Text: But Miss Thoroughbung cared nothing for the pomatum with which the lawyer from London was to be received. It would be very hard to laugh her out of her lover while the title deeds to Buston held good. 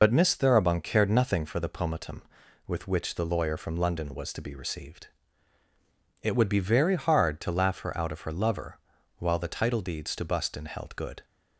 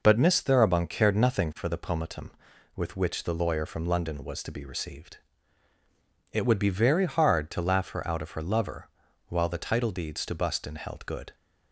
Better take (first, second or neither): second